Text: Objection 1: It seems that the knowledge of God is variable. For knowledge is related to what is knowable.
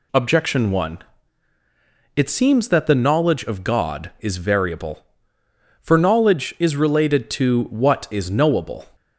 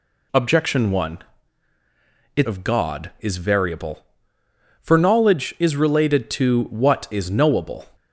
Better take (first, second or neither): first